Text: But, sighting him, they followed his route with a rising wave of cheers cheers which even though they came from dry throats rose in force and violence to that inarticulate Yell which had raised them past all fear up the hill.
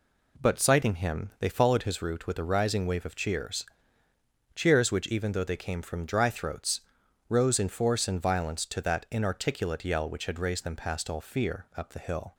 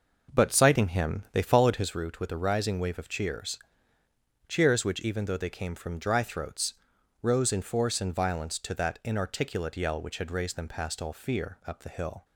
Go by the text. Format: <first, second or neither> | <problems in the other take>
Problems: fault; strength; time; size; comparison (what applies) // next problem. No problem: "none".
first | starts louder than the rest; noticeable; until 2.0 s; 5.5 dB // pauses between "cheers" and "cheers"; noticeable; at 3.5 s; 0.90 s long; noticeable in the first // pauses between "throats" and "rose"; noticeable; at 6.7 s; 0.48 s long; noticeable in the first